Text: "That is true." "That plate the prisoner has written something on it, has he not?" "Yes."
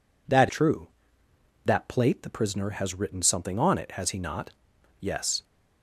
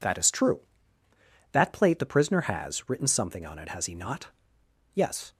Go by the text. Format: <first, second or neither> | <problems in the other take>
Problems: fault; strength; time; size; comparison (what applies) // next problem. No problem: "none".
second | skips "is"; at 0.4 s